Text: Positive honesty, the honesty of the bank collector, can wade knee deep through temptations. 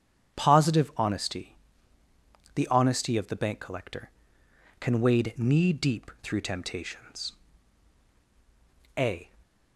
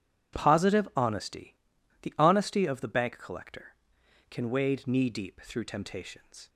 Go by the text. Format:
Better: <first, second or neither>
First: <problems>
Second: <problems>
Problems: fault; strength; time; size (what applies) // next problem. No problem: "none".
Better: second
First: starts louder than the rest; strong; until 1.4 s; 9 dB // goes on to say "A"; slight; from 8.9 s on; 0.32 s long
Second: none